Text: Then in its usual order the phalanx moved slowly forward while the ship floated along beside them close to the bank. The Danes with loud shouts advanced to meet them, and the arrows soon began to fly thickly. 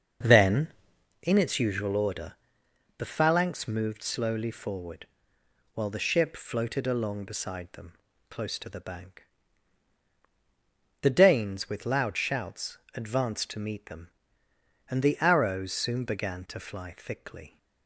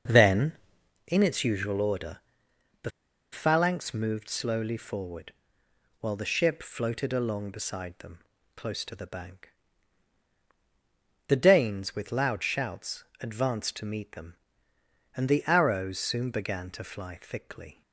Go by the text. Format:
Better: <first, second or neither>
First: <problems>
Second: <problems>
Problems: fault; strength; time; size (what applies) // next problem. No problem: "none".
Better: first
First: starts louder than the rest; until 1.7 s; 6 dB // pauses between "order" and "the"; noticeable; at 2.3 s; 0.66 s long // pauses between "forward" and "while"; noticeable; at 5.0 s; 0.66 s long // pauses between "them" and "close"; slight; at 7.9 s; 0.36 s long // pauses between "shouts" and "advanced"; slight; at 12.7 s; 0.16 s long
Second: starts louder than the rest; until 1.6 s; 6 dB // pauses between "order" and "the"; noticeable; at 2.1 s; 0.66 s long // pauses between "the" and "phalanx"; at 2.9 s; 0.42 s long // pauses between "forward" and "while"; noticeable; at 5.3 s; 0.66 s long // pauses between "them" and "close"; slight; at 8.1 s; 0.36 s long // pauses between "shouts" and "advanced"; slight; at 13.0 s; 0.16 s long